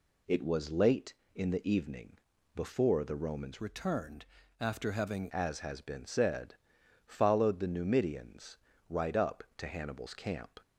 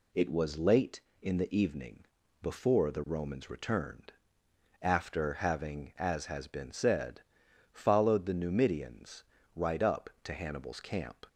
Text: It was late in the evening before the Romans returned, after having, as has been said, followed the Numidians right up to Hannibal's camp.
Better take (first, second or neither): second